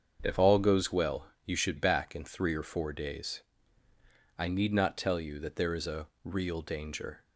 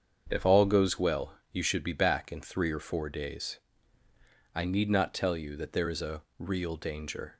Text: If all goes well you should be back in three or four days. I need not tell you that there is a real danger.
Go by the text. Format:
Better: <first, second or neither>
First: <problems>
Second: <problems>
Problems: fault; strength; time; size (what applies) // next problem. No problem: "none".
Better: second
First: starts louder than the rest; strong; until 1.2 s; 7 dB // pauses between "well" and "you"; slight; at 1.3 s; 0.16 s long // skips "be"; at 1.7 s // pauses between "a" and "real"; slight; at 6.0 s; 0.16 s long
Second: starts louder than the rest; strong; until 1.3 s; 7.5 dB // pauses between "well" and "you"; slight; at 1.3 s; 0.16 s long // pauses between "a" and "real"; slight; at 6.2 s; 0.16 s long